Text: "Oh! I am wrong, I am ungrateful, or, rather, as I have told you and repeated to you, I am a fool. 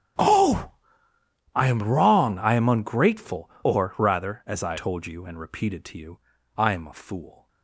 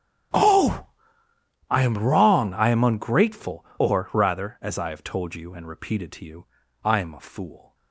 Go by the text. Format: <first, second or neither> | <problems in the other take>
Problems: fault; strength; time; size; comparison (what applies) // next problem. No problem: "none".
second | starts louder than the rest; strong; until 2.0 s; 10 dB; strong in the second // skips "have"; at 4.7 s